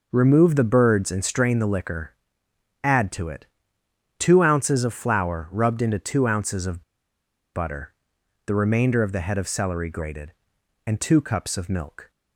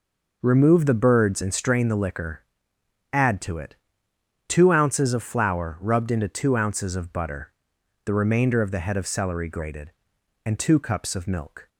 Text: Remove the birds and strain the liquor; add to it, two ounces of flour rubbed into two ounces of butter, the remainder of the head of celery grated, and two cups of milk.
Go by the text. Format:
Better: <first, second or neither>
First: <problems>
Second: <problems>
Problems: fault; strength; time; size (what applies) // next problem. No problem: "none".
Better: second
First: pauses between "of" and "butter"; noticeable; at 6.8 s; 0.72 s long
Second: none